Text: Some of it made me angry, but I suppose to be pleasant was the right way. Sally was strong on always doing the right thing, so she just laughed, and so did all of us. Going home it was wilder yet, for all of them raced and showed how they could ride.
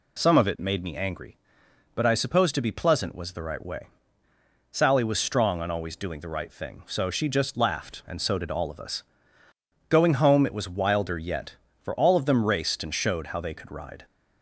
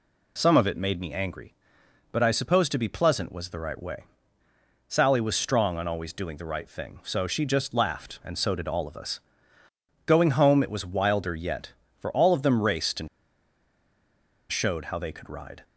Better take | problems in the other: first | pauses between "and" and "showed"; strong; at 13.0 s; 1.4 s long

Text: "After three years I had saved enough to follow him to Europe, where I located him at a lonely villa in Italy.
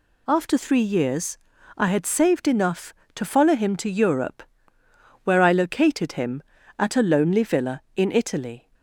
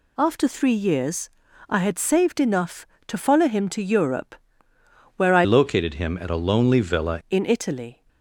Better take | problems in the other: first | pauses between "years" and "I"; at 1.2 s; 0.40 s long; also in the first // changes voice from "located" to "villa"; from 5.4 to 7.2 s; 1.8 s long

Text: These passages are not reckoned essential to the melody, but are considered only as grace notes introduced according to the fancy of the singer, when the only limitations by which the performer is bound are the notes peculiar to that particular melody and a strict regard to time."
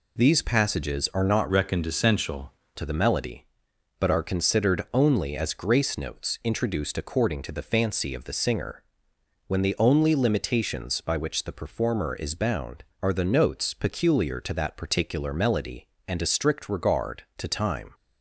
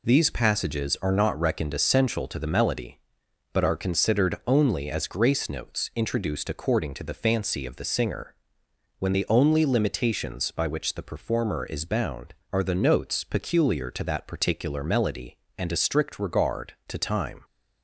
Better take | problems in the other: second | changes voice from "reckoned" to "essential"; from 1.4 to 2.5 s; 1.1 s long

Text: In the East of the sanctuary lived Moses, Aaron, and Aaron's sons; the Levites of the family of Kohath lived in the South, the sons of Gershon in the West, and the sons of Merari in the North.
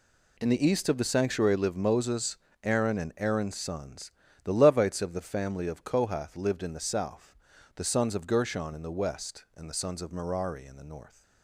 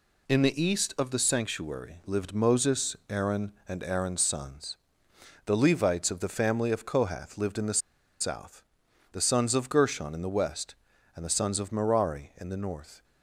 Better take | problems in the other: first | pauses between "the" and "South"; at 7.7 s; 0.40 s long

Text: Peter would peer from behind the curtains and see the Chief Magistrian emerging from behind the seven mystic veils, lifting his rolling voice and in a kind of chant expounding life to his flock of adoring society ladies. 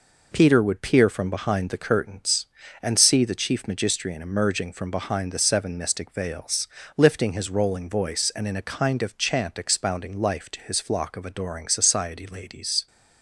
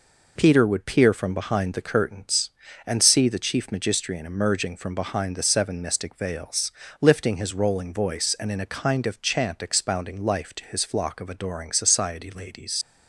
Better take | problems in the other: first | leaves "ladies" unfinished; at 12.8 s; 90 ms

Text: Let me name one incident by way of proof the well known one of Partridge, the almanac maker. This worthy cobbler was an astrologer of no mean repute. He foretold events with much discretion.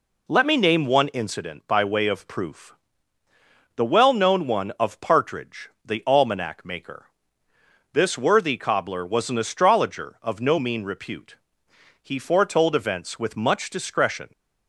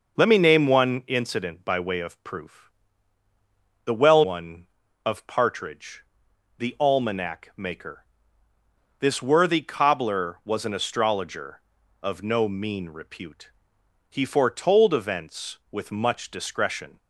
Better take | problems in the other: first | pauses between "proof" and "the"; at 2.7 s; 1.1 s long; also in the first // skips "known"; at 4.2 s

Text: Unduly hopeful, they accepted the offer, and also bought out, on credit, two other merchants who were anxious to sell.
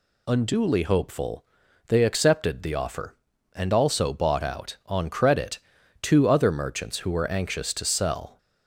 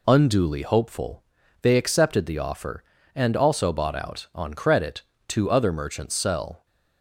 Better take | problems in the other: first | skips "who were anxious to"; at 6.1 s

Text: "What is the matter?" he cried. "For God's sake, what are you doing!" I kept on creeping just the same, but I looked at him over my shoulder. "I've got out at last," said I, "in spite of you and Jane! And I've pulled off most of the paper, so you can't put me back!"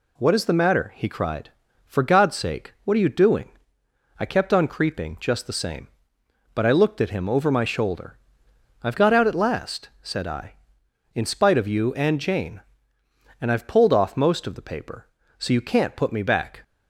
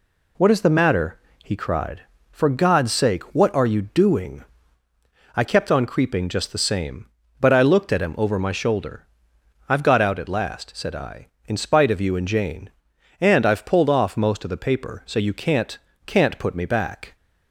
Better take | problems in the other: first | says "can't" twice; at 16.0 s

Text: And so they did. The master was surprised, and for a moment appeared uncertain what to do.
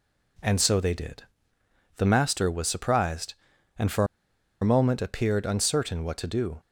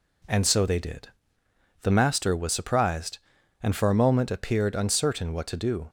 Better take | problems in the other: second | pauses between "for" and "a"; noticeable; at 4.0 s; 0.56 s long

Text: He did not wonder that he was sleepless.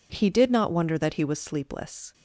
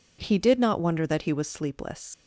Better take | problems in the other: first | leaves "sleepless" unfinished; at 2.1 s; 75 ms

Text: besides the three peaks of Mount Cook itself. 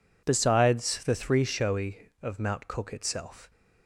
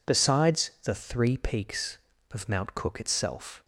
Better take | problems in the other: second | says "showy" for "peaks"; at 1.4 s

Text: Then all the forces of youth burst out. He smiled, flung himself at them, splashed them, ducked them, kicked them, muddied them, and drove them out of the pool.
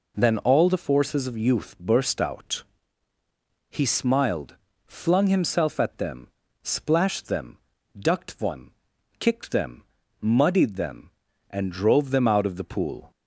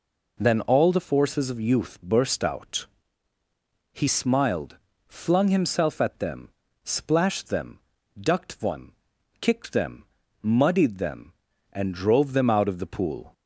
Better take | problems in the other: neither | none

